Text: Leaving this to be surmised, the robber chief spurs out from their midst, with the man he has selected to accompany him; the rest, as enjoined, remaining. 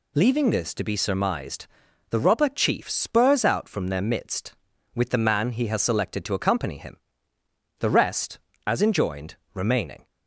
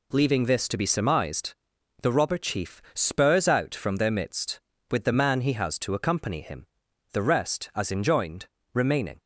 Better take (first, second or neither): first